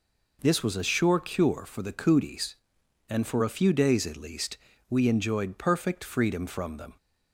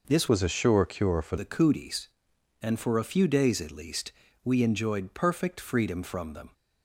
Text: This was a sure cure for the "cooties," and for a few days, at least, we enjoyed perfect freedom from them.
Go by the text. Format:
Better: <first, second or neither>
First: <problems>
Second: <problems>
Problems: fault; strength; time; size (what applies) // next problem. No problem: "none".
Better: first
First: none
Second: changes voice from "was" to "for"; from 0.2 to 1.3 s; 1.1 s long